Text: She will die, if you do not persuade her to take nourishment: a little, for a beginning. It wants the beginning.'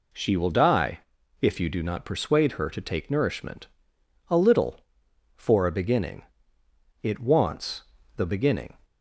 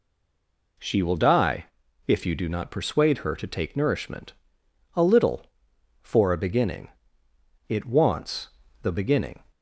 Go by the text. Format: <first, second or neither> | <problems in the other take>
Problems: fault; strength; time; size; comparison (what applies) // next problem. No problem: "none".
first | stays silent before the first word; slight; until 0.7 s; 0.7 s long // pauses between "wants" and "the"; slight; at 8.4 s; 0.34 s long; slight in the first